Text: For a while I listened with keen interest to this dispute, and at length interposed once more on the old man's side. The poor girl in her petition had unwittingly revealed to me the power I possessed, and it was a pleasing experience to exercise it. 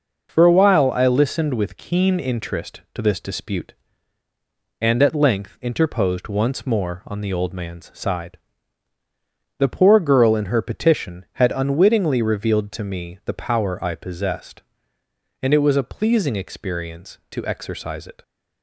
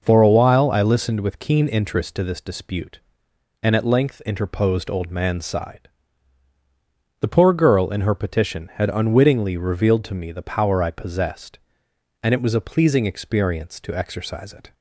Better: first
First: none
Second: skips "once more on the"; at 4.8 s

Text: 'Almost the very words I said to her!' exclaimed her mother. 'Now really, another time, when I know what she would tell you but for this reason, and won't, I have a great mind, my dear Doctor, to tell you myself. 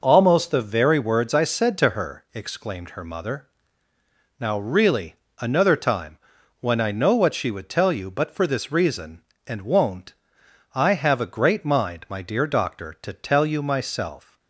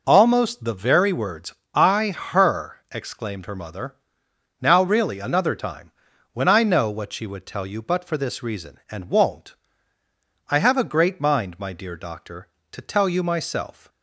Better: first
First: none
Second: pauses between "words" and "I"; slight; at 1.5 s; 0.18 s long // skips "said to"; at 2.1 s

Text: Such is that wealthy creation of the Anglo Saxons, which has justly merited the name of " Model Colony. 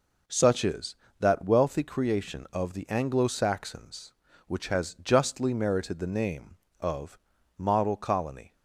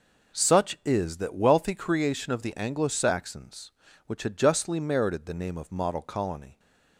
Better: first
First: none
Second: says "had" for "has"; at 4.2 s

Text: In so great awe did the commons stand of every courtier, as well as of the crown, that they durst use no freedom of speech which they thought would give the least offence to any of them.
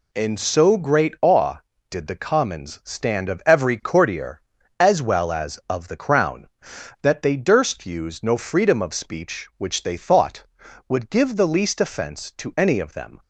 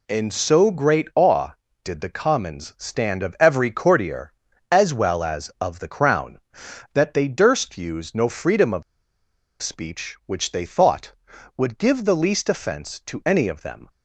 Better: first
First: none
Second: pauses between "of" and "speech"; noticeable; at 8.8 s; 0.79 s long

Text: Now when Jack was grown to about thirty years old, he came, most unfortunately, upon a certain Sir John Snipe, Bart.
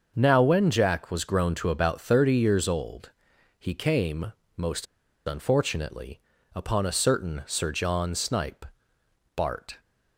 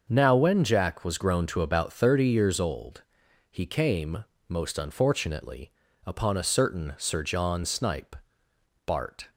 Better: second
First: starts louder than the rest; until 1.1 s; 6.5 dB // pauses between "most" and "unfortunately"; at 4.8 s; 0.41 s long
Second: starts louder than the rest; until 1.1 s; 6.5 dB

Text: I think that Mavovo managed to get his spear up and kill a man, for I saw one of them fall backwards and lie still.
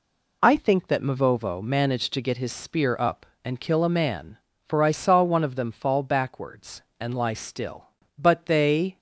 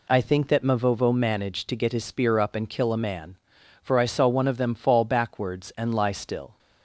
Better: second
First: goes on to say "But they"; noticeable; from 8.1 s on; 0.80 s long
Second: none

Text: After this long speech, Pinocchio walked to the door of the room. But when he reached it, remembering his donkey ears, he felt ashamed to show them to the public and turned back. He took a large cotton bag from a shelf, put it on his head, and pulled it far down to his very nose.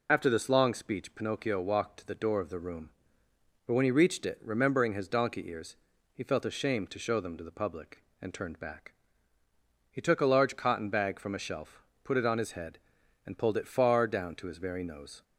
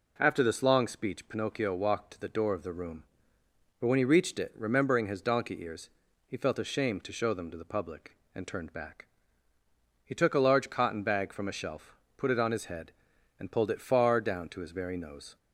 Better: second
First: loses the start of "After"; at 0.0 s; 65 ms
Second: none

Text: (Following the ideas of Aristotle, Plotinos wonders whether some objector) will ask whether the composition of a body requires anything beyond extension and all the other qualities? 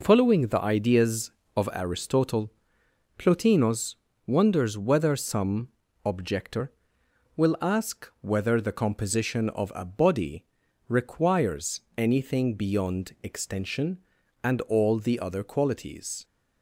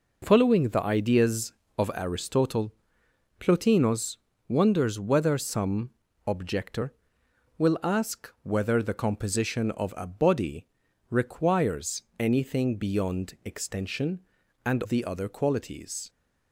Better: first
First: pauses between "Plotinos" and "wonders"; slight; at 3.9 s; 0.32 s long // pauses between "some" and "objector"; slight; at 5.6 s; 0.36 s long // pauses between "body" and "requires"; at 10.4 s; 0.44 s long // pauses between "requires" and "anything"; slight; at 11.8 s; 0.18 s long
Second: pauses between "Plotinos" and "wonders"; slight; at 4.1 s; 0.32 s long // pauses between "some" and "objector"; slight; at 5.8 s; 0.36 s long // pauses between "body" and "requires"; at 10.6 s; 0.44 s long // pauses between "requires" and "anything"; slight; at 12.0 s; 0.18 s long // skips "all"; at 14.8 s

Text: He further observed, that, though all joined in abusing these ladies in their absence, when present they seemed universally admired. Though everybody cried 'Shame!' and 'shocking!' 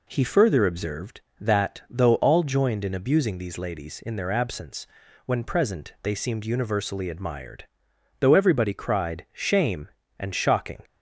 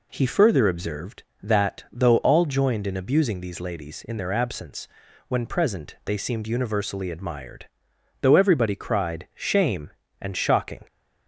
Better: neither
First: none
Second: none

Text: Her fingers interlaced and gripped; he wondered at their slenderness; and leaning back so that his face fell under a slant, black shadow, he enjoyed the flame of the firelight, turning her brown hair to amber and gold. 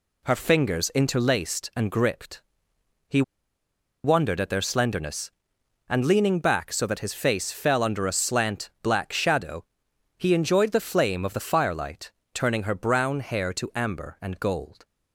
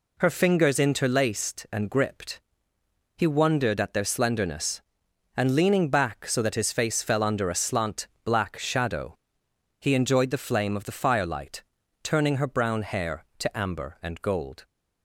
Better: second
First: pauses between "he" and "wondered"; noticeable; at 3.2 s; 0.81 s long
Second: none

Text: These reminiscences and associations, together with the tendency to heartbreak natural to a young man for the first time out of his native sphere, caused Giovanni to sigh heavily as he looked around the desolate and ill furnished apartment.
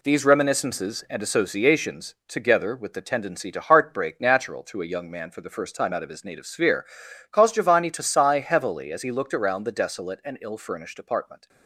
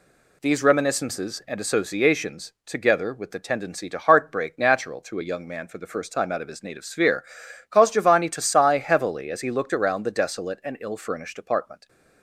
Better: second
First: gets quieter; throughout; 6.5 dB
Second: none

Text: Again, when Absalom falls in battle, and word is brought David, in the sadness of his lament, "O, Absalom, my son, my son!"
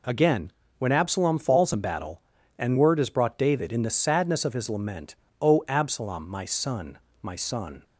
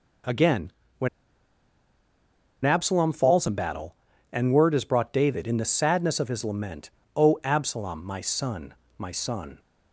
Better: first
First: none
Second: pauses between "when" and "Absalom"; strong; at 1.0 s; 1.5 s long

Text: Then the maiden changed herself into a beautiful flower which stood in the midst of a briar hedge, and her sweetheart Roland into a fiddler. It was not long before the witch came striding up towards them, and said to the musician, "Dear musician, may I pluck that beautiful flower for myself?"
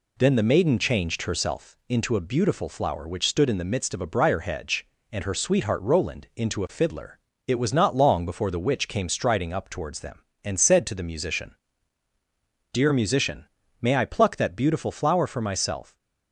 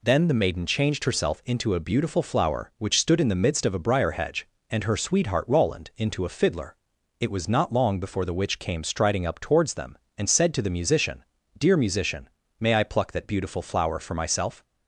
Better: neither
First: none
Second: none

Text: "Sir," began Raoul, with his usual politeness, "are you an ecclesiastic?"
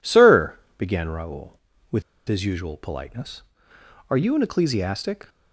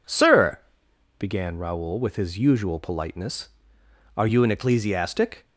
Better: second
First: pauses between "with" and "his"; slight; at 2.0 s; 0.26 s long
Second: none

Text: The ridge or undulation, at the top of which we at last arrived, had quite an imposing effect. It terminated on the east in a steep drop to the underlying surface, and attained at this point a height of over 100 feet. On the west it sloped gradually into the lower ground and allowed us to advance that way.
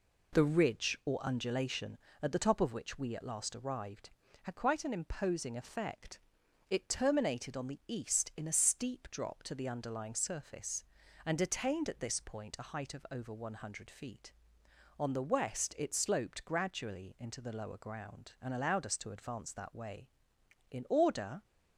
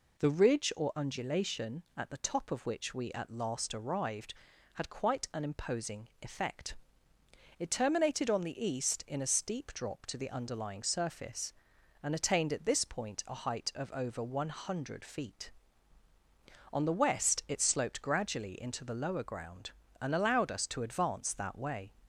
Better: second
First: goes on to say "In order"; noticeable; from 20.7 s on; 0.72 s long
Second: none

